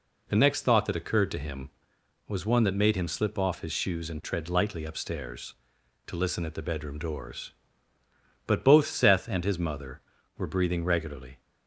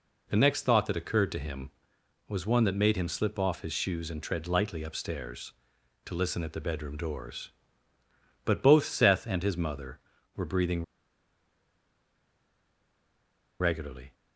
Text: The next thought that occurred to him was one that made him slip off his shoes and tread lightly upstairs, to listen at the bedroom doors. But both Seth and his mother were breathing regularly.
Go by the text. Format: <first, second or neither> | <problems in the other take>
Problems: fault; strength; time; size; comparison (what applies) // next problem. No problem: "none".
first | pauses between "breathing" and "regularly"; strong; at 10.8 s; 2.7 s long